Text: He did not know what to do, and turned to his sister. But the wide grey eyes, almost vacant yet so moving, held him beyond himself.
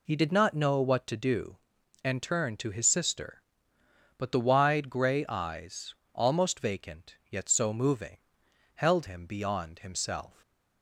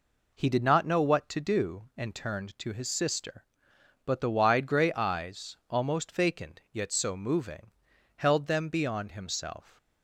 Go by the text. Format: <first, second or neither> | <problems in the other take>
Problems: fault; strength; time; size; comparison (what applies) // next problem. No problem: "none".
first | says "them" for "him"; at 8.4 s